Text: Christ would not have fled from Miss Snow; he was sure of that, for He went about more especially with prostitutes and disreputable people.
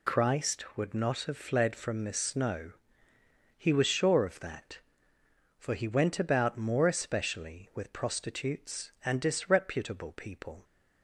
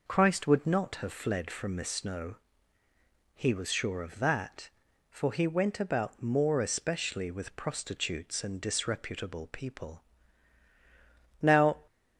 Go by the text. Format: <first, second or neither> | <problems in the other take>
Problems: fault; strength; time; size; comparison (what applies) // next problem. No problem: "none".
first | goes on to say "Now"; slight; from 11.4 s on; 0.38 s long